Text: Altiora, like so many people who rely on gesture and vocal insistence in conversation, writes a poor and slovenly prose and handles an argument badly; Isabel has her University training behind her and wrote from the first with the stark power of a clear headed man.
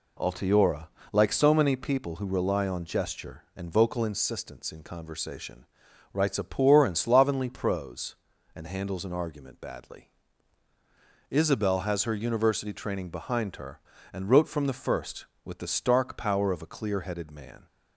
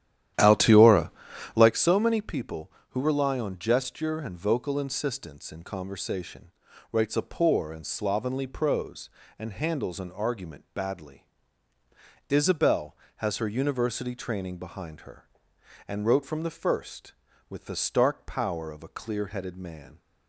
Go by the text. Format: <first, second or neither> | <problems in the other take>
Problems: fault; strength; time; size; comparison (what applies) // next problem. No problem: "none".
first | starts louder than the rest; strong; until 1.8 s; 11.5 dB